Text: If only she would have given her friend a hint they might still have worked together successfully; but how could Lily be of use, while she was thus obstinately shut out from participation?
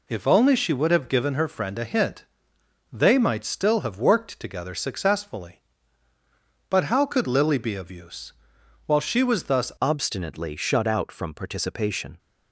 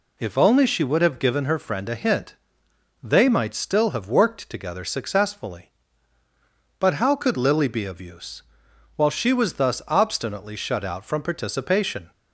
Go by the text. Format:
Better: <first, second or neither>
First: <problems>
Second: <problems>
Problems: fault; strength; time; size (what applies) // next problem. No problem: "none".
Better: second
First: pauses between "hint" and "they"; noticeable; at 2.2 s; 0.70 s long // changes voice at "obstinately"; from 9.8 s on; 2.3 s long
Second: pauses between "hint" and "they"; noticeable; at 2.3 s; 0.70 s long